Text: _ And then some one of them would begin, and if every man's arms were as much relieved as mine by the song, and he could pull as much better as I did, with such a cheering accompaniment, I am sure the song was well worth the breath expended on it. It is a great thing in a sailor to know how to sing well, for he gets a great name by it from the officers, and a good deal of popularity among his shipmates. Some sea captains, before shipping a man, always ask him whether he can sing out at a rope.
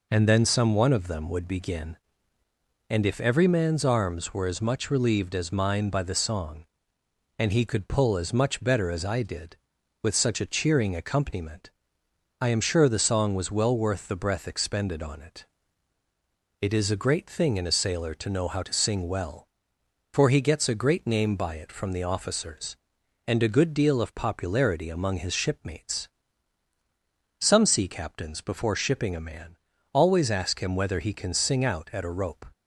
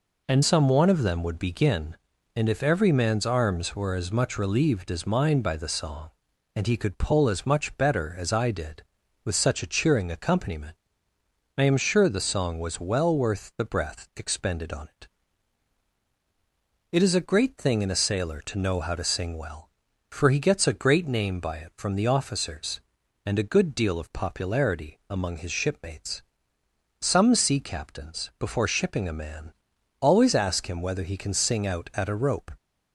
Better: first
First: none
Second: skips "then"; at 0.4 s

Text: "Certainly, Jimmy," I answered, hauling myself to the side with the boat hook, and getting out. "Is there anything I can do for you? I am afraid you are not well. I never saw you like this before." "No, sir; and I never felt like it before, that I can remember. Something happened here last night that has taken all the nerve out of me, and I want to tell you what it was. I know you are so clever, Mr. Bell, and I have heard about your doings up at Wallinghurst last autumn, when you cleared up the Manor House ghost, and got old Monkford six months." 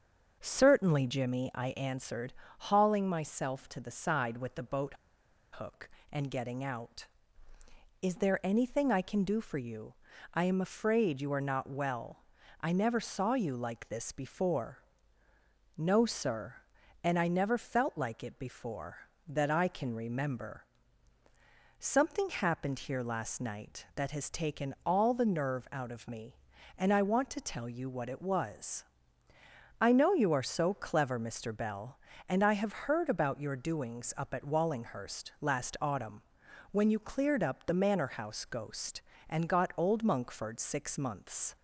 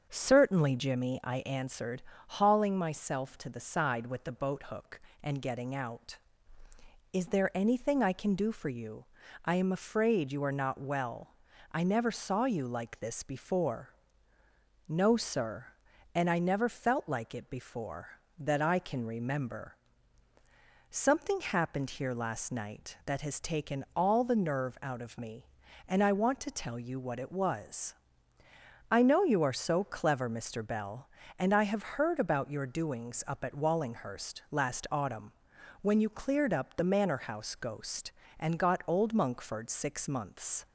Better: second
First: starts louder than the rest; until 1.4 s; 7 dB // pauses between "boat" and "hook"; noticeable; at 4.9 s; 0.57 s long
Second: starts louder than the rest; until 1.1 s; 7 dB

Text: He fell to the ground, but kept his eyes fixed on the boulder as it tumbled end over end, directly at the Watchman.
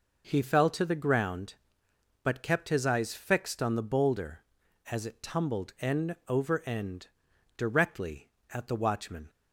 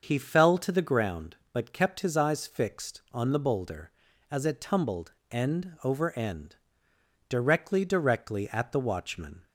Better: first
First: none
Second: starts louder than the rest; until 1.0 s; 6.5 dB // pauses between "tumbled" and "end"; slight; at 5.1 s; 0.20 s long // says "directly" twice; at 7.8 s

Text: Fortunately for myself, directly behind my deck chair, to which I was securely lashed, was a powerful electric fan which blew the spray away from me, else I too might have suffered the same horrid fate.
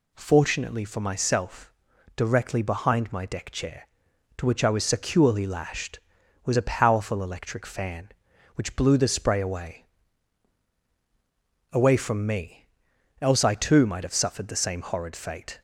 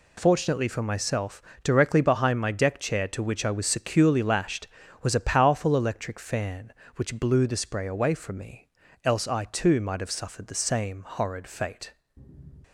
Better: second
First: says "away" twice; at 11.7 s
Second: none

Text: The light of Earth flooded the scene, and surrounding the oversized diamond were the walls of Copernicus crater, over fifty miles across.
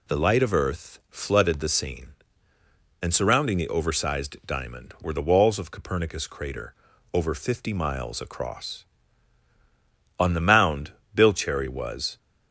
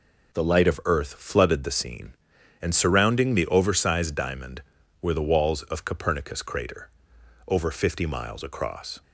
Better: second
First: goes on to say "On the mound Bill Cherry was"; strong; from 10.1 s on; 2.0 s long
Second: none

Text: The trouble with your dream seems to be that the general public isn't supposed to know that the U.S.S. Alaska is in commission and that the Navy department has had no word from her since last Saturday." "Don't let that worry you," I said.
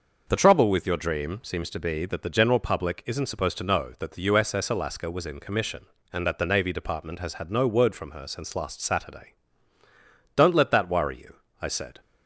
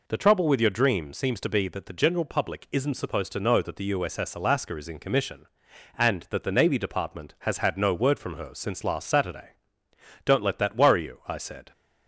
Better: second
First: says "was" for "is"; at 5.1 s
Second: none

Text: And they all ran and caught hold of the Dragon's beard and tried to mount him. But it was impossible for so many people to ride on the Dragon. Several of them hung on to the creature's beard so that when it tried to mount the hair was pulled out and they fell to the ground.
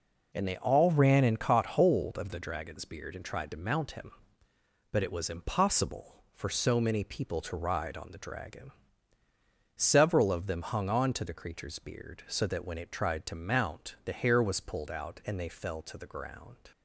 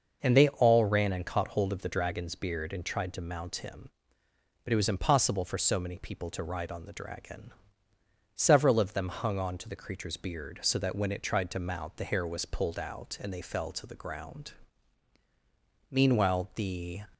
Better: first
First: none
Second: starts louder than the rest; noticeable; until 1.2 s; 6 dB // goes on to say "Meanwhile the"; noticeable; from 15.9 s on; 1.1 s long

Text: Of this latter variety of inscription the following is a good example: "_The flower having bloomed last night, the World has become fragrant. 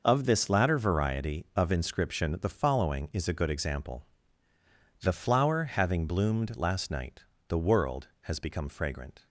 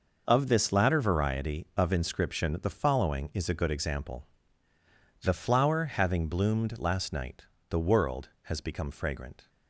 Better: neither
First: none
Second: none

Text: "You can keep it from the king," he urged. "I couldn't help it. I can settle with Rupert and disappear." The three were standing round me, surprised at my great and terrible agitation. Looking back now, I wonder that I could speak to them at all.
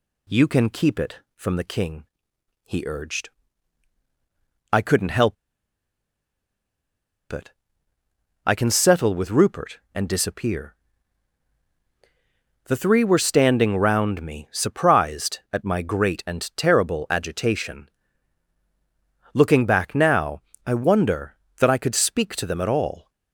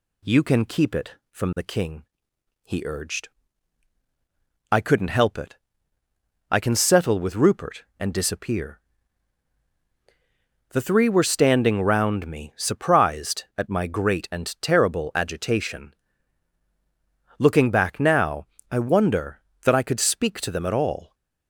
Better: second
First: pauses between "help" and "it"; strong; at 5.3 s; 1.9 s long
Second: none

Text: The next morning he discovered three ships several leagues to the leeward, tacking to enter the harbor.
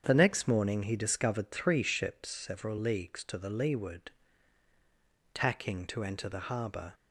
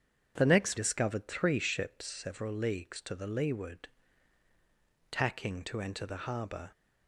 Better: first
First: starts louder than the rest; strong; until 1.0 s; 7.5 dB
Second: starts louder than the rest; strong; until 1.3 s; 7.5 dB // skips "morning he"; at 0.7 s

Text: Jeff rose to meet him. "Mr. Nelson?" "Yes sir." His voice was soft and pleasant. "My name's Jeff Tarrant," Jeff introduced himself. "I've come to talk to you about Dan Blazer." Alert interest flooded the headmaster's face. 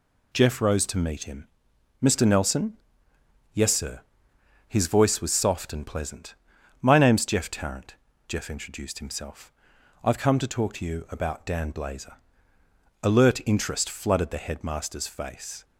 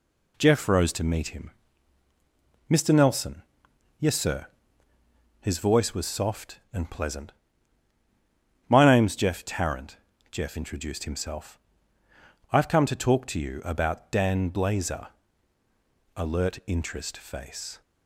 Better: first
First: none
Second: skips "flooded the headmaster's"; at 17.1 s

